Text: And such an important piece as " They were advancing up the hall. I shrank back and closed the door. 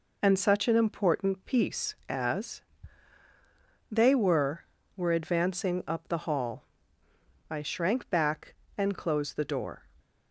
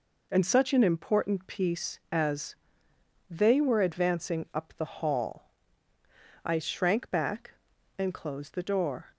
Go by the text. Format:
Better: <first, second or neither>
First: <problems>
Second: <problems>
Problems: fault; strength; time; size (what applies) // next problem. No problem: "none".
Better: second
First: says "were" twice; at 4.9 s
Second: none